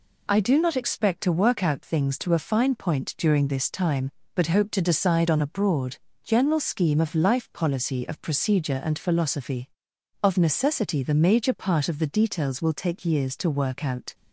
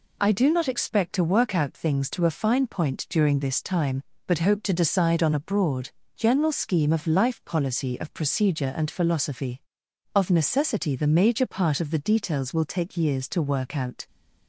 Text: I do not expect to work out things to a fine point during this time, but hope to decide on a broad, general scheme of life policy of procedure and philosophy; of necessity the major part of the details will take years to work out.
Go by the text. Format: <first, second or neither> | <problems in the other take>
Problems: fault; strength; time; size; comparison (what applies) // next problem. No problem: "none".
neither | none